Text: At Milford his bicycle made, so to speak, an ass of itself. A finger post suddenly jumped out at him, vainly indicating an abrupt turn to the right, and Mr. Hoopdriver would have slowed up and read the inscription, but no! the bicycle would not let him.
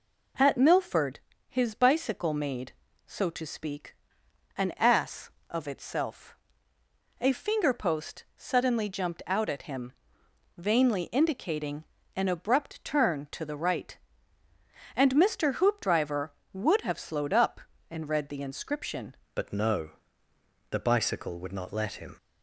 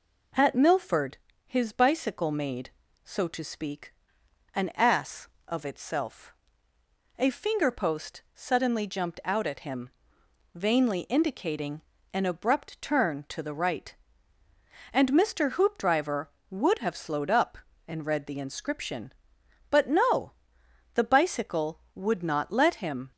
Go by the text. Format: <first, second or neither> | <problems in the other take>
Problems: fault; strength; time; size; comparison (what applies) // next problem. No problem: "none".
second | pauses between "Milford" and "his"; slight; at 1.1 s; 0.28 s long; slight in the second // pauses between "indicating" and "an"; slight; at 11.8 s; 0.30 s long; slight in the second // changes voice at "but"; from 19.3 s on; 2.8 s long